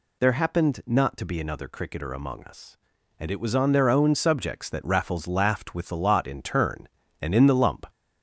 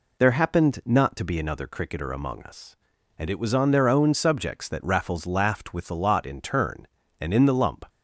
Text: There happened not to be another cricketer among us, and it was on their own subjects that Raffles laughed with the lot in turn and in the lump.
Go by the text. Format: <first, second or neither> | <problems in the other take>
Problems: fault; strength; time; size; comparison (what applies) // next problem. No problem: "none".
second | gets louder; slight; throughout; 3 dB